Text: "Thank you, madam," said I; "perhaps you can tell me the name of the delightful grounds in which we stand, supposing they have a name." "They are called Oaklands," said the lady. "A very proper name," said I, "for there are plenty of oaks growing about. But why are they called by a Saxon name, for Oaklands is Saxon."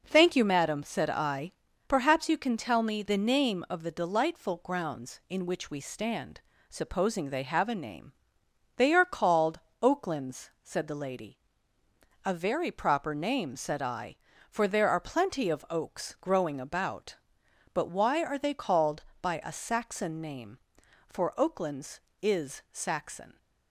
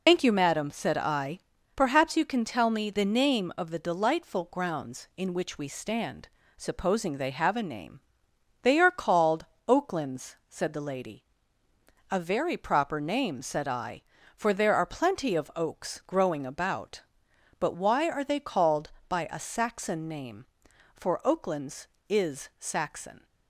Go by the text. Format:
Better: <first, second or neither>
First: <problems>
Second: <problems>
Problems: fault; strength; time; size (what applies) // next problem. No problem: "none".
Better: first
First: pauses between "called" and "Oaklands"; slight; at 9.5 s; 0.22 s long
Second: loses the start of "Thank"; at 0.0 s; 145 ms // pauses between "called" and "Oaklands"; slight; at 9.4 s; 0.22 s long